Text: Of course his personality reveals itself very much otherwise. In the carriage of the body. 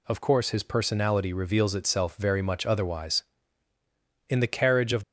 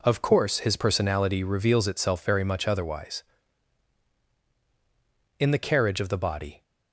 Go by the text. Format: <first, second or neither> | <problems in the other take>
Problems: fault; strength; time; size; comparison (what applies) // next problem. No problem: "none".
second | stops before "the body"; at 5.0 s